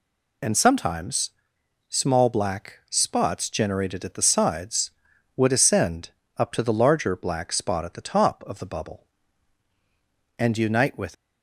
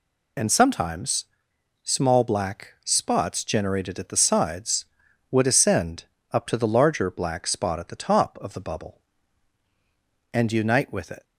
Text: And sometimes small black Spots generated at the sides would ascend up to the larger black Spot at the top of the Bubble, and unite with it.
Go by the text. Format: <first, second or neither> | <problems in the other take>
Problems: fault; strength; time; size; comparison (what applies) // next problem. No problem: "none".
second | pauses between "sometimes" and "small"; noticeable; at 1.3 s; 0.58 s long; noticeable in the second // pauses between "ascend" and "up"; slight; at 6.0 s; 0.28 s long; slight in the second // stops before "it"; at 11.1 s